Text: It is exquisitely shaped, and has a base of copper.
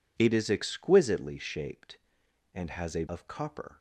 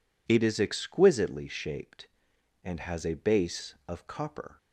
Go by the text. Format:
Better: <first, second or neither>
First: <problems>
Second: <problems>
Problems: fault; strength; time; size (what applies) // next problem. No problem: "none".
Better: second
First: skips "base"; at 3.0 s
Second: none